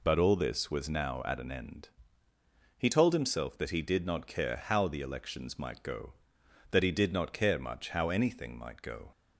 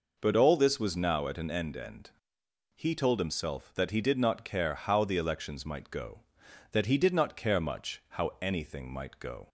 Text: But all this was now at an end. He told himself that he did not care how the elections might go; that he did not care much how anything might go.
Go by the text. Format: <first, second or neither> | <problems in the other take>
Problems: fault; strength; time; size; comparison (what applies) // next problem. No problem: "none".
first | says "end" twice; at 1.7 s